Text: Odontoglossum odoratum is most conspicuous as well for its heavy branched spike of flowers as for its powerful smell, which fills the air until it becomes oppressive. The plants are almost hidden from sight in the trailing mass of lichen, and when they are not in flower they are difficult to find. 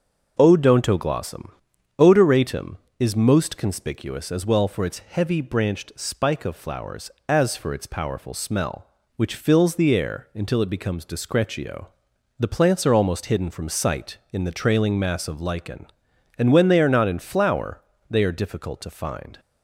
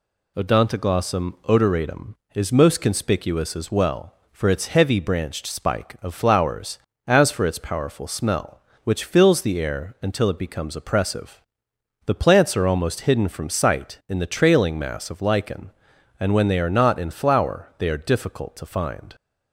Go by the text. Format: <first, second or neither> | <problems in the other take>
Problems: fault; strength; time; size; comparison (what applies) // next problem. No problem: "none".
second | starts louder than the rest; until 1.3 s; 6 dB // pauses between "Odontoglossum" and "odoratum"; noticeable; at 1.4 s; 0.48 s long // says "discretio" for "oppressive"; at 11.0 s // pauses between "flower" and "they"; slight; at 17.7 s; 0.28 s long